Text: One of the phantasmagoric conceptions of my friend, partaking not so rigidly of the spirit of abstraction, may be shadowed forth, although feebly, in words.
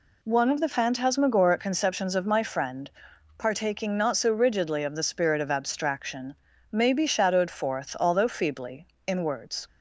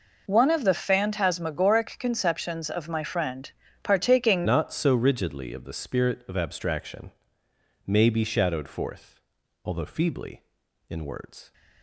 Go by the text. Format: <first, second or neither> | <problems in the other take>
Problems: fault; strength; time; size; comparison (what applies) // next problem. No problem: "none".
first | changes voice at "not"; from 4.4 s on; 7.1 s long